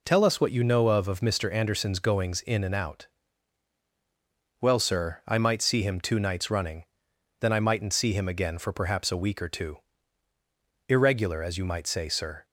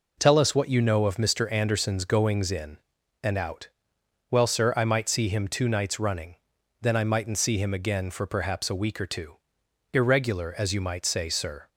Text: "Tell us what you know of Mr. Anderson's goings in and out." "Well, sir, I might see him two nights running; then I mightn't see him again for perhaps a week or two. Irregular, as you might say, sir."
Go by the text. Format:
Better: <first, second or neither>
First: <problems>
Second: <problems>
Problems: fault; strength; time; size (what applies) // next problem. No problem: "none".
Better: second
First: says "of" twice; at 1.0 s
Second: none